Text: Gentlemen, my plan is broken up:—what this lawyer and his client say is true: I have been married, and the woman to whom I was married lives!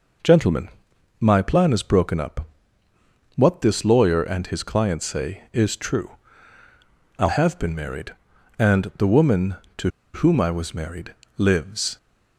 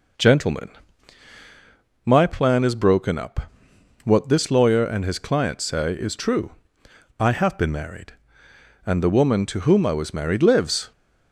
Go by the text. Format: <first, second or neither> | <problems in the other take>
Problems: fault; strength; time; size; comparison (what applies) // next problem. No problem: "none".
second | pauses between "to" and "whom"; slight; at 9.8 s; 0.26 s long // pauses between "married" and "lives"; slight; at 11.1 s; 0.22 s long